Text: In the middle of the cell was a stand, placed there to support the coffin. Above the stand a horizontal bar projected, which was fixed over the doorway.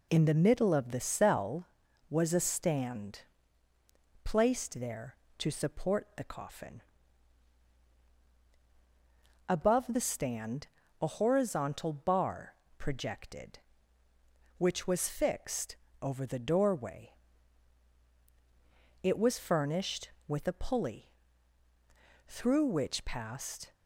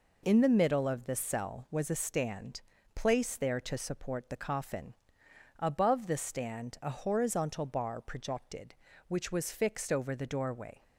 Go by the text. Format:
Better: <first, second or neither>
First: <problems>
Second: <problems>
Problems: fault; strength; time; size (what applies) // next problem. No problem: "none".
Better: second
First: pauses between "stand" and "a"; slight; at 10.6 s; 0.34 s long // pauses between "bar" and "projected"; slight; at 12.5 s; 0.24 s long // pauses between "fixed" and "over"; slight; at 15.7 s; 0.26 s long // goes on to say "It was furnished with a pulley through which passed"; strong; from 19.0 s on; 4.7 s long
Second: none